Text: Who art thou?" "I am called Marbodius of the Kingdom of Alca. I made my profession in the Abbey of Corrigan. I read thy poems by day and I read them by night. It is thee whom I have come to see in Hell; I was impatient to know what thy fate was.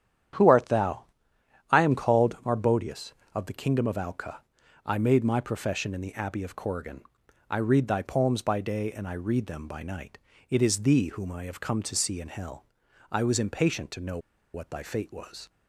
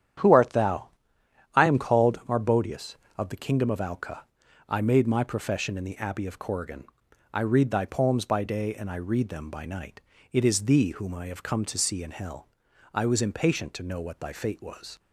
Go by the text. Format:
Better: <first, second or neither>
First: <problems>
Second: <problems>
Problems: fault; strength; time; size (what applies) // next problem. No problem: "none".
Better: second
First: starts louder than the rest; strong; until 1.9 s; 10 dB // pauses between "know" and "what"; slight; at 14.1 s; 0.35 s long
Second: starts louder than the rest; strong; until 1.8 s; 9.5 dB